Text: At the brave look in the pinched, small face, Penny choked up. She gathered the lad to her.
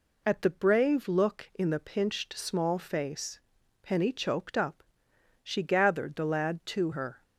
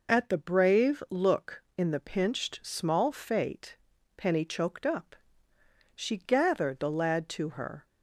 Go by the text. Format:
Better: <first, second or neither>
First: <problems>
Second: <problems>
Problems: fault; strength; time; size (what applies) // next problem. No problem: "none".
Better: first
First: none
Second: says "fate" for "face"; at 3.1 s